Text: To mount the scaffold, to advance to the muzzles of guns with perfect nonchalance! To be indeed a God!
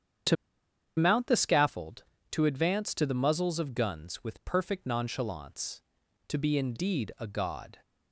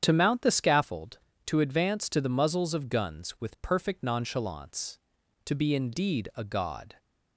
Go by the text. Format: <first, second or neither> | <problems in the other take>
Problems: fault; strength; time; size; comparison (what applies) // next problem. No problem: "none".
second | starts louder than the rest; strong; until 1.8 s; 8.5 dB; strong in the second // pauses between "To" and "mount"; noticeable; at 0.3 s; 0.61 s long